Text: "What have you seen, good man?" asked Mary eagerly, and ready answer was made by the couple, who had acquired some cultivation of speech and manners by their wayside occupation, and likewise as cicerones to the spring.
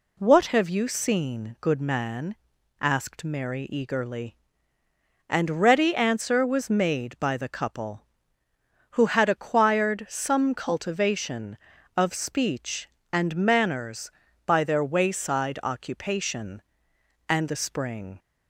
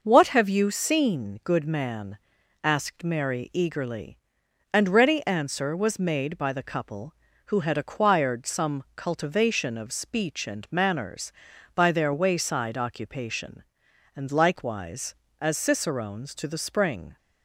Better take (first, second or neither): second